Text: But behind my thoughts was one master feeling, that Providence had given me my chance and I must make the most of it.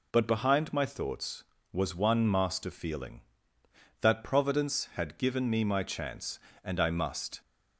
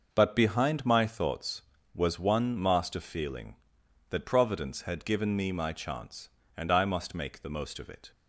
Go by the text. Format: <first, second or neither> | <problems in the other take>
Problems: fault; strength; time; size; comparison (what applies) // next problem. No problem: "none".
second | stops before "make the most of it"; at 7.4 s